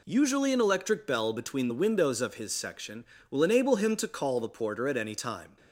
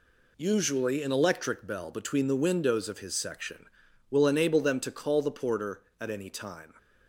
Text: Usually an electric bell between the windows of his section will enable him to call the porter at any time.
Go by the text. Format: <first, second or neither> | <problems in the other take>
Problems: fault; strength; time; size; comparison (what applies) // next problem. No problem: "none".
first | says "them" for "him"; at 4.6 s